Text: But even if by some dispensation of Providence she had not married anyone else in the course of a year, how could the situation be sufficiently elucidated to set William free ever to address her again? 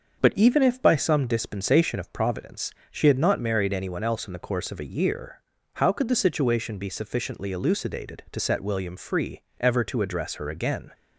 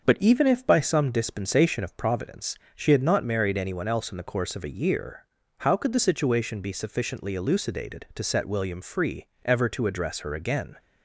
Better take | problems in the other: neither | starts louder than the rest; the same in both // pauses between "Providence" and "she"; slight; the same in both // pauses between "free" and "ever"; slight; the same in both

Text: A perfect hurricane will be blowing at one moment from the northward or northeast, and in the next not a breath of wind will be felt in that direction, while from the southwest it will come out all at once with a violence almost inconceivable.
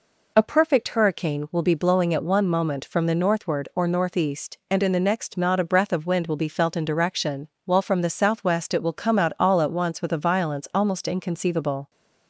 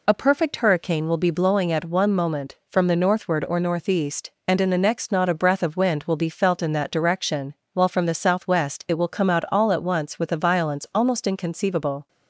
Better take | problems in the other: second | skips "that"; at 6.8 s

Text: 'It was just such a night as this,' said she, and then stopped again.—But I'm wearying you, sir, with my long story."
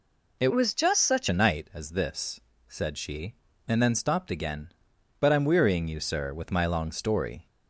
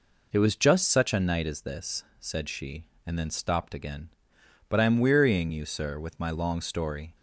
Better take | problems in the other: second | changes voice from "was" to "such"; from 0.5 to 1.2 s; 0.7 s long

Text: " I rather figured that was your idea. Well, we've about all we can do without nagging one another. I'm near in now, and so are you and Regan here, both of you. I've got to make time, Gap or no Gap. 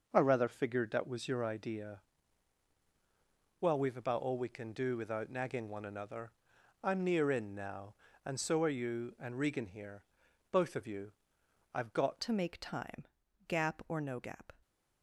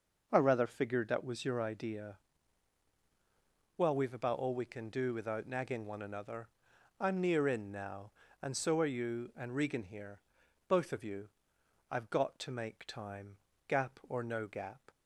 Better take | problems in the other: second | changes voice at "to"; from 12.2 s on; 2.3 s long // stays silent after the last word; slight; from 14.5 s on; 0.5 s long

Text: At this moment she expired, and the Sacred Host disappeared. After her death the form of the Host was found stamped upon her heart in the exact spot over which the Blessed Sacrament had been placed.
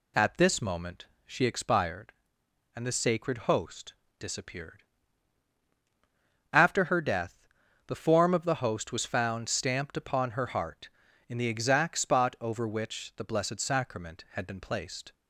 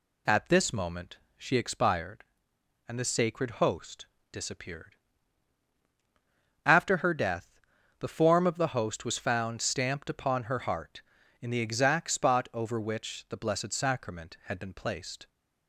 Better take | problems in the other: neither | pauses between "moment" and "she"; slight; the same in both // pauses between "Host" and "disappeared"; slight; the same in both // pauses between "death" and "the"; the same in both

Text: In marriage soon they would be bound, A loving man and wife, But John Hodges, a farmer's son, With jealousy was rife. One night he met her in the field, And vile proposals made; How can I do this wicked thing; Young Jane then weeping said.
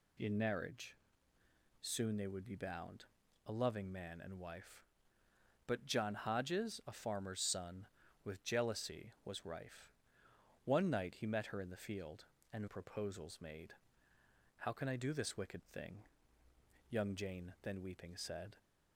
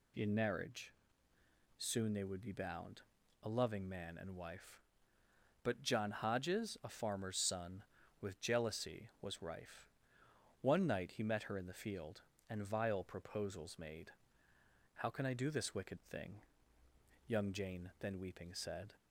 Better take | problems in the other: second | pauses between "marriage" and "soon"; noticeable; at 0.9 s; 0.84 s long; noticeable in the second // skips "vile"; at 12.6 s

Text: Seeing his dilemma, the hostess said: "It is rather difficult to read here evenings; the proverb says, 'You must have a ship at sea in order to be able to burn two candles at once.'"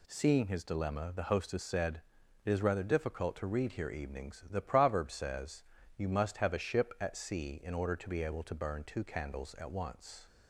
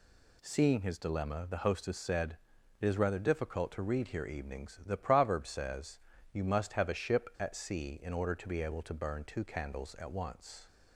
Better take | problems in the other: neither | none

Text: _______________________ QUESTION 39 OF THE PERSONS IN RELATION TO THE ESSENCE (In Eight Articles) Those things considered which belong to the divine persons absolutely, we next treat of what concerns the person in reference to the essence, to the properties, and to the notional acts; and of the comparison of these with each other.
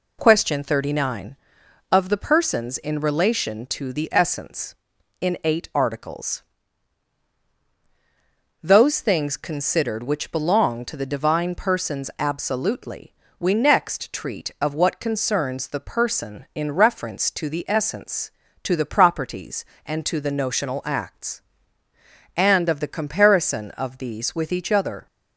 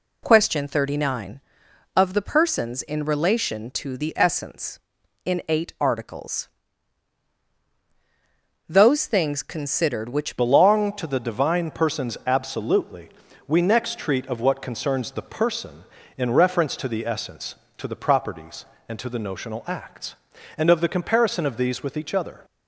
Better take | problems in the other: first | changes voice at "belong"; from 10.3 s on; 12.1 s long

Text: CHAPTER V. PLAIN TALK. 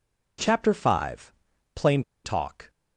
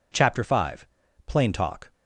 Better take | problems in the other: second | pauses between "PLAIN" and "TALK"; slight; at 2.0 s; 0.23 s long

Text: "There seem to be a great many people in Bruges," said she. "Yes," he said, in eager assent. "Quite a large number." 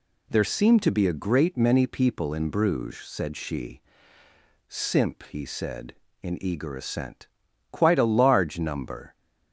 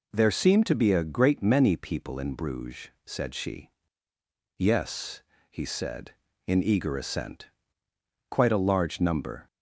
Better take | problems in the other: second | says "Simp" for "Yes"; at 4.6 s

